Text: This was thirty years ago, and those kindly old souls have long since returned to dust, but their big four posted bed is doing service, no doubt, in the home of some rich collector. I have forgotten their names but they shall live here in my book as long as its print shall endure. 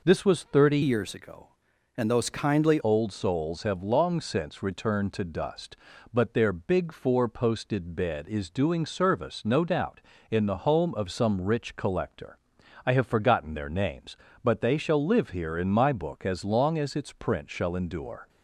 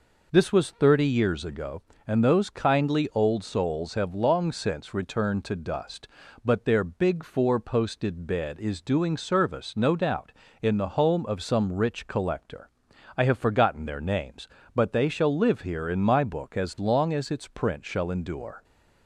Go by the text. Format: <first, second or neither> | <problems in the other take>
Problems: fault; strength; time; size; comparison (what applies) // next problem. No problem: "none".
second | changes voice from "years" to "kindly"; from 0.8 to 2.7 s; 1.9 s long